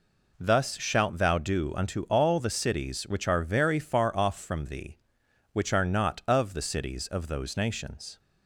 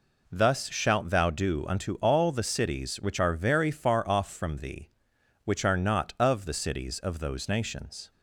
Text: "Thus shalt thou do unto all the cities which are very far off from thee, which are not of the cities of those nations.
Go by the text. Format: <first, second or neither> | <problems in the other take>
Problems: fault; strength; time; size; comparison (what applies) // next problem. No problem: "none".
neither | none